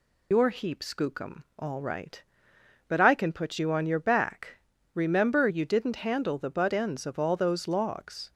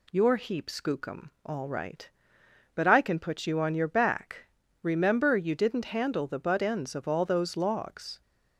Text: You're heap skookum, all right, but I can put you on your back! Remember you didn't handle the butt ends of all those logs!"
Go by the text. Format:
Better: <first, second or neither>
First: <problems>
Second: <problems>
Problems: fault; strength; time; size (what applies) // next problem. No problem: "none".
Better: second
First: loses the start of "You're"; at 0.3 s; 100 ms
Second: none